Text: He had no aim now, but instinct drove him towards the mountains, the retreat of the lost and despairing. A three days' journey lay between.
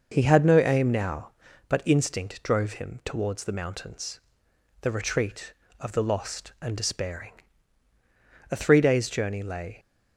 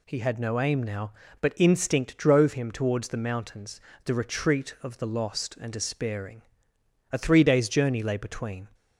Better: second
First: stops before "between"; at 9.7 s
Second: none

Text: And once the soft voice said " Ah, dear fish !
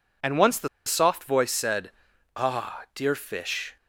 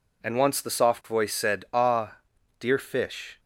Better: second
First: pauses between "the" and "soft"; slight; at 0.6 s; 0.17 s long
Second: none

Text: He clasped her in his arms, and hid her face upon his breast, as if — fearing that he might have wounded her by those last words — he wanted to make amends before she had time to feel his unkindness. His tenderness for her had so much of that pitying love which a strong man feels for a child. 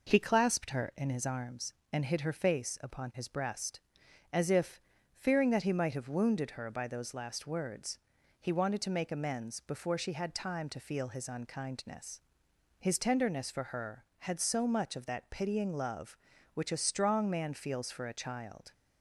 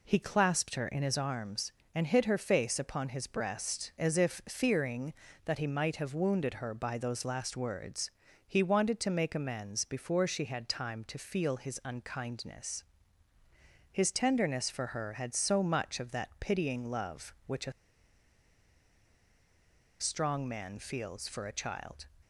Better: first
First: none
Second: pauses between "a" and "strong"; strong; at 17.7 s; 2.2 s long

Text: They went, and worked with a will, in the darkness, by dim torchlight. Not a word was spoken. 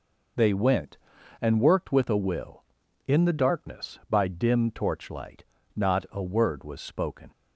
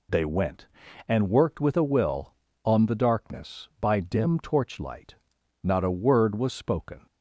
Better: first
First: none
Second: says "on" for "in"; at 2.6 s

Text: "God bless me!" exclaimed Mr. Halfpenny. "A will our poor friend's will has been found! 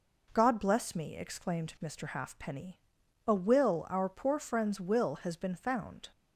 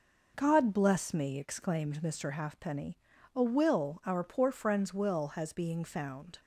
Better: first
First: none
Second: says "being" for "been"; at 5.5 s

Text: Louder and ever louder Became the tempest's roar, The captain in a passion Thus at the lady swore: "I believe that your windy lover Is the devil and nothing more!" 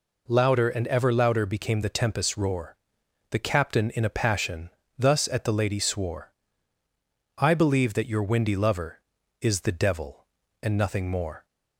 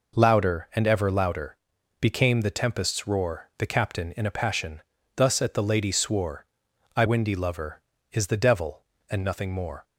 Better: first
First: pauses between "passion" and "Thus"; slight; at 4.6 s; 0.28 s long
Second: pauses between "louder" and "Became"; at 1.5 s; 0.44 s long // pauses between "passion" and "Thus"; slight; at 4.8 s; 0.36 s long // skips "believe that your"; at 7.0 s

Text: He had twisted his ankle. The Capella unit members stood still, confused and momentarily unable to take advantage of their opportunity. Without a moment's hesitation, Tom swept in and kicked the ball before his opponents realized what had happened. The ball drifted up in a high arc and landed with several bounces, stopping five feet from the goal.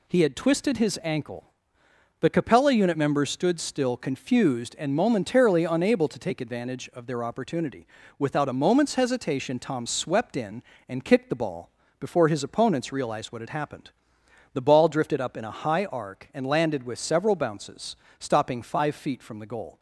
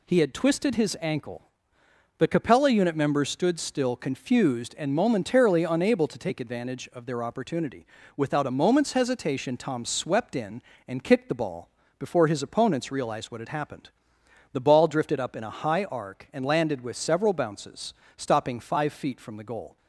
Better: neither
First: pauses between "ball" and "before"; slight; at 11.7 s; 0.28 s long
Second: pauses between "ball" and "before"; slight; at 11.6 s; 0.28 s long

